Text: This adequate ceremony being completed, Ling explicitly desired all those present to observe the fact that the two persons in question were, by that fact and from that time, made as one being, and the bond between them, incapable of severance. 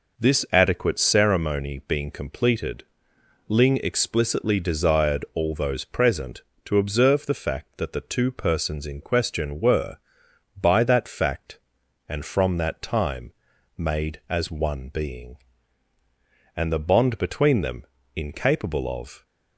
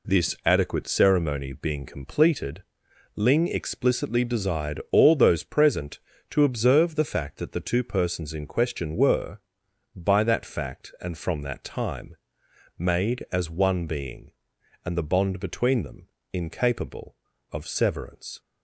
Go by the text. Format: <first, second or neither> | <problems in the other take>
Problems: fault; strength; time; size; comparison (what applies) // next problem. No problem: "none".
second | stops before "severance"; at 19.2 s